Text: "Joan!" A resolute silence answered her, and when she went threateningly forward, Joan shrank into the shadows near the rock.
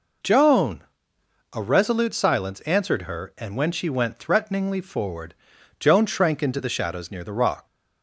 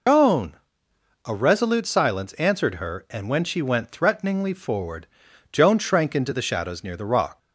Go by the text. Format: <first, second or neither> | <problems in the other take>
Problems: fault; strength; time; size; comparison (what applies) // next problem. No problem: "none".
first | loses the start of "Joan"; at 0.0 s; 105 ms